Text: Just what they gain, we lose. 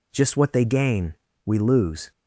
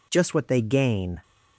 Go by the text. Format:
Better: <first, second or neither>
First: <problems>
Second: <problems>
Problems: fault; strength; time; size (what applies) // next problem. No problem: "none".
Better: first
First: none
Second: stops before "we lose"; at 1.2 s